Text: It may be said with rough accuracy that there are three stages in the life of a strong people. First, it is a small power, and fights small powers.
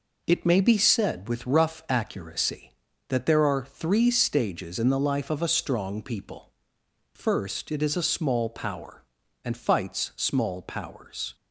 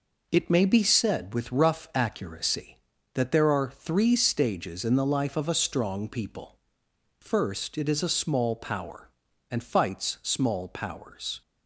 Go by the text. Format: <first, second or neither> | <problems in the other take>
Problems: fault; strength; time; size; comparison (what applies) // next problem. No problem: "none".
neither | none